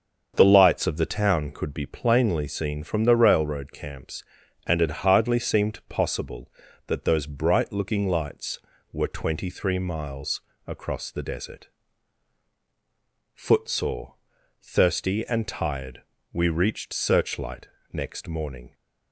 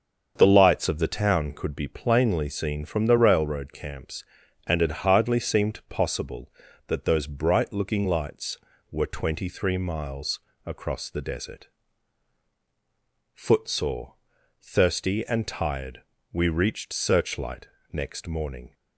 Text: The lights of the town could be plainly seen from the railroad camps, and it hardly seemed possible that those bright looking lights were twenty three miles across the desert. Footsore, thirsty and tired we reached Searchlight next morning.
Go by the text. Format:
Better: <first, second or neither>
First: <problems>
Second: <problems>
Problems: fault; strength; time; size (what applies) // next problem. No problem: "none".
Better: neither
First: starts louder than the rest; until 1.3 s; 7 dB // pauses between "miles" and "across"; slight; at 10.4 s; 0.26 s long // pauses between "tired" and "we"; slight; at 16.0 s; 0.30 s long // pauses between "Searchlight" and "next"; slight; at 17.6 s; 0.24 s long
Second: starts louder than the rest; until 1.3 s; 7 dB // pauses between "miles" and "across"; slight; at 10.3 s; 0.26 s long // pauses between "tired" and "we"; slight; at 16.0 s; 0.30 s long // pauses between "Searchlight" and "next"; slight; at 17.6 s; 0.24 s long